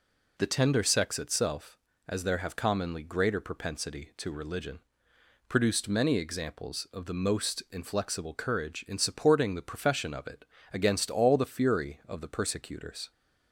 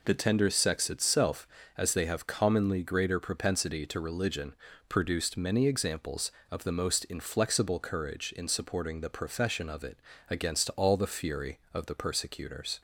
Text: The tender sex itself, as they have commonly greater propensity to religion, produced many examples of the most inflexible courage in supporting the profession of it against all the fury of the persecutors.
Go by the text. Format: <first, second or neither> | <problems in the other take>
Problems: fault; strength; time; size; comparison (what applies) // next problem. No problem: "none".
second | says "there" for "they"; at 2.2 s // pauses between "it" and "against"; slight; at 10.4 s; 0.28 s long; slight in the second